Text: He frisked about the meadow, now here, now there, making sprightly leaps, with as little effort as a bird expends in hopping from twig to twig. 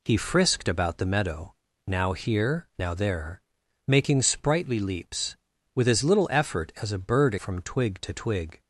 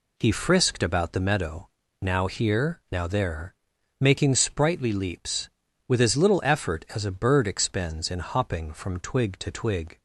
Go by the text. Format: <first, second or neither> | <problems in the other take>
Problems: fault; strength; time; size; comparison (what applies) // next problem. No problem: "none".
second | skips "expends in hopping"; at 7.3 s